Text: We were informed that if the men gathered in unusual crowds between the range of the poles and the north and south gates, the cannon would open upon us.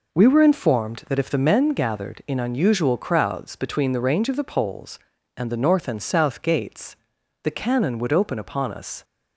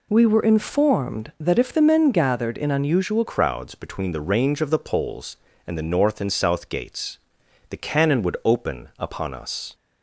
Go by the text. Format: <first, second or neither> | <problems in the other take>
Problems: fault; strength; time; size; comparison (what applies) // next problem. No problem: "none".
first | changes voice at "crowds"; from 3.2 s on; 6.5 s long